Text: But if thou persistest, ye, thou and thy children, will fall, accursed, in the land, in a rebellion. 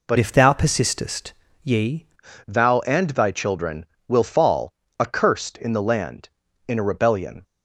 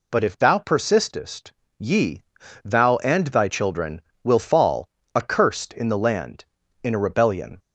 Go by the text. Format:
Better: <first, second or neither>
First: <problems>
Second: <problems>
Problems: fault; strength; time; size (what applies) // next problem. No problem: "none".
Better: second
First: changes voice from "if" to "ye"; from 0.1 to 2.0 s; 1.9 s long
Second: none